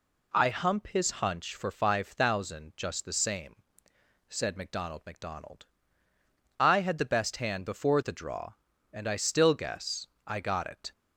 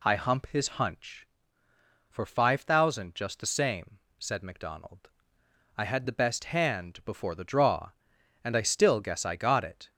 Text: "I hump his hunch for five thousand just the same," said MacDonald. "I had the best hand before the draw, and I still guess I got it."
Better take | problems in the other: second | says "MacDonald" twice; at 5.0 s // pauses between "guess" and "I"; slight; at 10.0 s; 0.18 s long

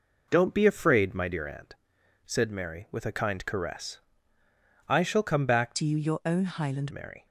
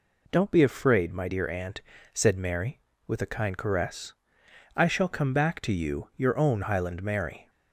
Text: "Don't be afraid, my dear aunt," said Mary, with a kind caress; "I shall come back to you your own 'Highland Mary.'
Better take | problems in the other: second | changes voice from "to" to "Highland"; from 5.7 to 6.9 s; 1.2 s long

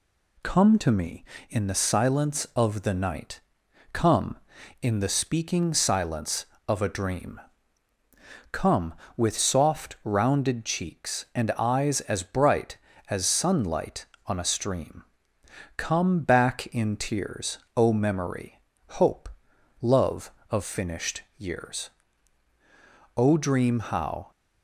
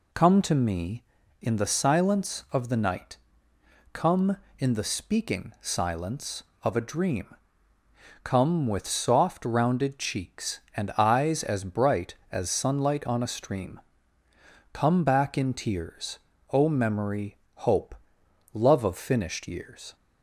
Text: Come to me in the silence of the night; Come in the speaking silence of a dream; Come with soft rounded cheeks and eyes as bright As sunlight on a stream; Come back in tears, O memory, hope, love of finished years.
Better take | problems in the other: second | goes on to say "O dream how"; noticeable; from 23.1 s on; 1.1 s long

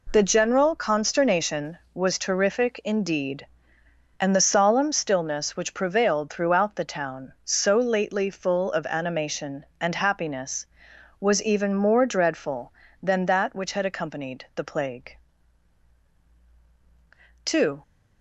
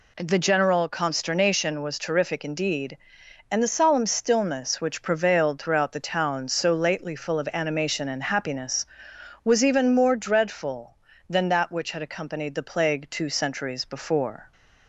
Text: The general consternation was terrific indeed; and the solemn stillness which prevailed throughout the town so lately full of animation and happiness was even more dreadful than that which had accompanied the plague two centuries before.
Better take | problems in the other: second | pauses between "plague" and "two"; strong; at 15.1 s; 2.2 s long // stops before "centuries before"; at 17.8 s

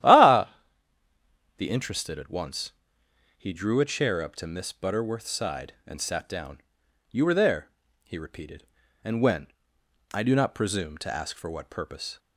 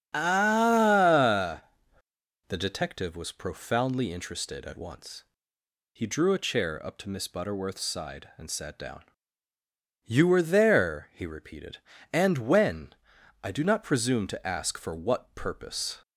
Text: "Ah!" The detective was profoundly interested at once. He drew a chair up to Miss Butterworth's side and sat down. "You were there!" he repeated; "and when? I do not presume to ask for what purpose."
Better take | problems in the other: second | starts louder than the rest; strong; until 2.0 s; 12 dB; strong in the second // skips "detective was profoundly"; at 1.6 s

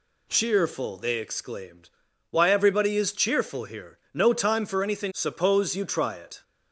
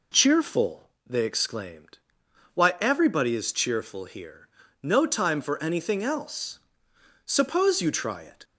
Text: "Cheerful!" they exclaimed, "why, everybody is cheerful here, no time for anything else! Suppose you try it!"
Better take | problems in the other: second | skips "else"; at 5.1 s

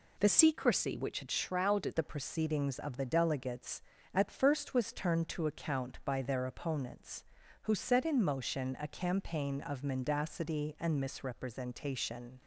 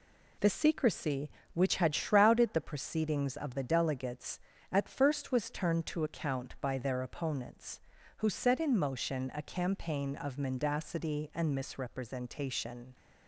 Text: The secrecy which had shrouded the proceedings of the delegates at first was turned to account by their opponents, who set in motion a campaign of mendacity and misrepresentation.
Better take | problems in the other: second | changes voice from "secrecy" to "shrouded"; from 0.2 to 1.9 s; 1.7 s long

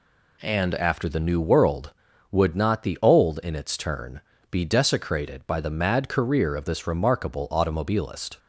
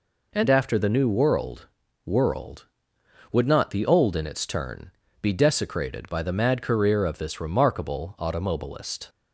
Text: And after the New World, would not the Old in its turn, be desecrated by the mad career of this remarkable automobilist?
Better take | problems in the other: first | says "World" twice; at 2.0 s

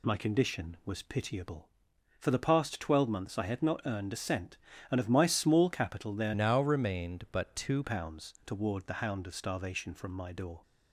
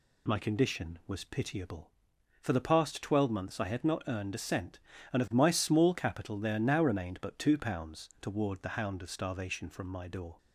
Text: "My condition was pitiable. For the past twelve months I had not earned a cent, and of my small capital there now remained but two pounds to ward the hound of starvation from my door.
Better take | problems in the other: second | changes voice from "now" to "two"; from 6.3 to 7.8 s; 1.5 s long

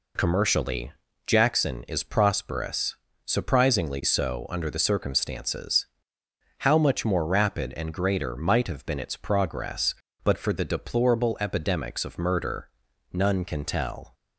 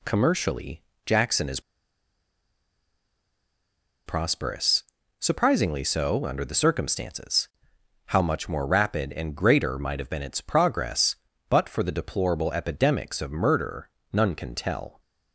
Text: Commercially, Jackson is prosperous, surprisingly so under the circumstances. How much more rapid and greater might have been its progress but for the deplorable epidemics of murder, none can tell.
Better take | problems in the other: first | pauses between "is" and "prosperous"; strong; at 1.5 s; 2.4 s long

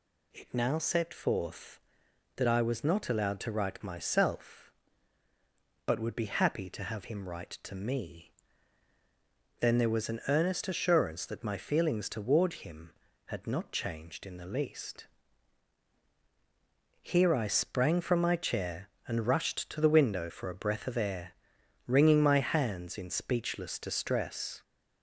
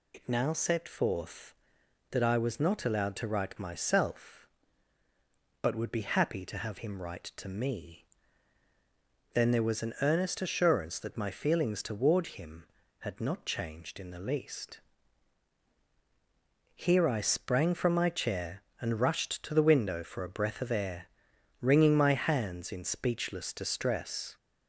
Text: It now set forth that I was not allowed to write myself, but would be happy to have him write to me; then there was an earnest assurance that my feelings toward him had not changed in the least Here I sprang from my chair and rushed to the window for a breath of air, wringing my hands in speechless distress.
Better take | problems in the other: first | loses the start of "It"; at 0.1 s; 75 ms // pauses between "least" and "Here"; strong; at 14.8 s; 1.9 s long; strong in the first

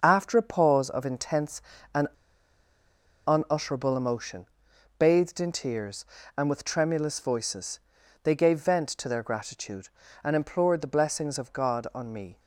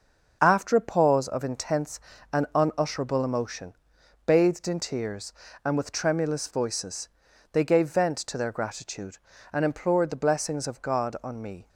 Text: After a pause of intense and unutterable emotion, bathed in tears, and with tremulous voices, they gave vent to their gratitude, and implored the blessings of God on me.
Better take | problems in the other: second | starts louder than the rest; until 1.0 s; 6.5 dB; also in the second // pauses between "and" and "unutterable"; at 2.0 s; 1.1 s long

